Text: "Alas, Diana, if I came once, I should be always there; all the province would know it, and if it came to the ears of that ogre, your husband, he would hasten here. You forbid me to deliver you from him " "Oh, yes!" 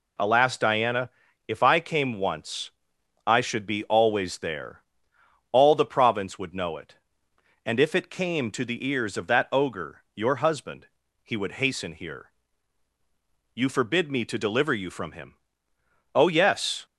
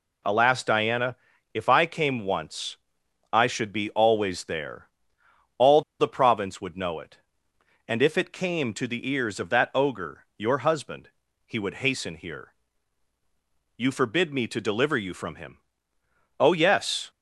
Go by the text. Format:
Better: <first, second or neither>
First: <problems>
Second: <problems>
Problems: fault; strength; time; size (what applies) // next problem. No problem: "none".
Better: first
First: none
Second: pauses between "all" and "the"; slight; at 5.8 s; 0.18 s long